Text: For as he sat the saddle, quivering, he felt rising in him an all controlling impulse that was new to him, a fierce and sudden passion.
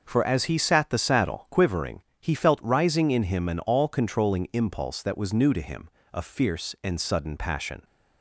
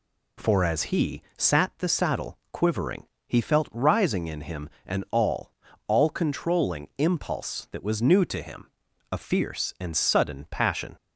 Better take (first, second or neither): first